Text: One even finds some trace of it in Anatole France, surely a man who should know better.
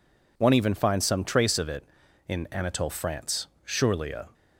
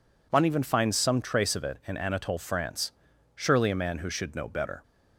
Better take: second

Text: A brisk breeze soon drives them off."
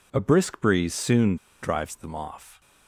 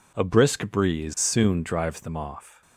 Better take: second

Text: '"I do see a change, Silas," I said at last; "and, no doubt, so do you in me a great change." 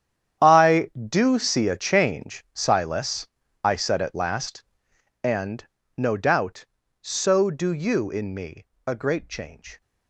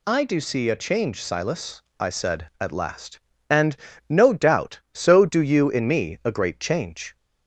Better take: second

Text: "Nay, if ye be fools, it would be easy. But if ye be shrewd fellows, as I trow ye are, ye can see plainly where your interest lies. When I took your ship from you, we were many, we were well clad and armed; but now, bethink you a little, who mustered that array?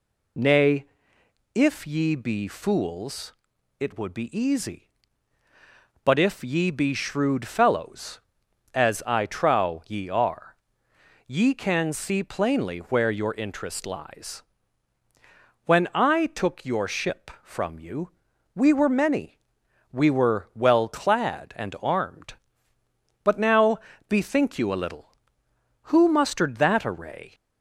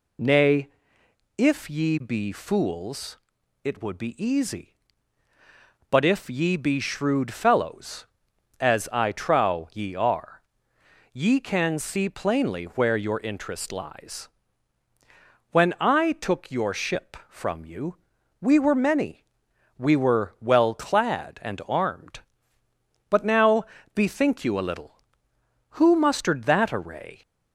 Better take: neither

